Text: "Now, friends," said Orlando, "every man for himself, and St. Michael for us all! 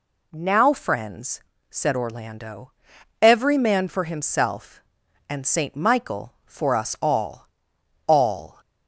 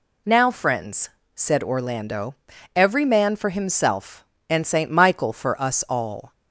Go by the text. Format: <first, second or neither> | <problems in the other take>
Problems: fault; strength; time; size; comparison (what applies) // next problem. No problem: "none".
second | says "all" twice; at 8.0 s